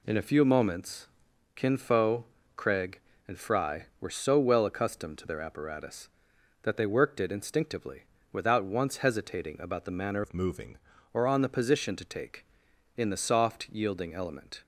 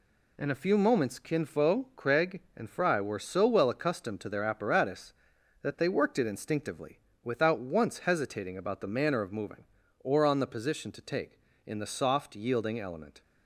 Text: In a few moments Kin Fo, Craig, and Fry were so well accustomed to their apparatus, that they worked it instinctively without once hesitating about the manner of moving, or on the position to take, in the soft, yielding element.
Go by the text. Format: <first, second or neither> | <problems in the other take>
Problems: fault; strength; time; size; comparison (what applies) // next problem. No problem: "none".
second | pauses between "moments" and "Kin"; noticeable; at 1.0 s; 0.48 s long // pauses between "instinctively" and "without"; slight; at 8.0 s; 0.28 s long; slight in the second // changes voice from "of" to "moving"; from 10.2 to 10.7 s; 0.5 s long